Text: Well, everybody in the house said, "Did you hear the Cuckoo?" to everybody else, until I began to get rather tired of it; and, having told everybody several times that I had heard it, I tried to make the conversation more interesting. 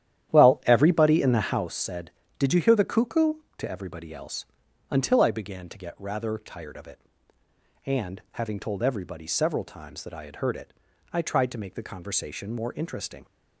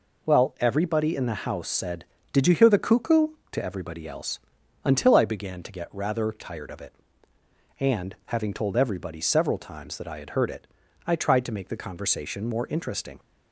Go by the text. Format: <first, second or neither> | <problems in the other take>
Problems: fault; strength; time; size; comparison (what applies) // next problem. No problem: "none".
second | starts louder than the rest; strong; until 1.8 s; 11 dB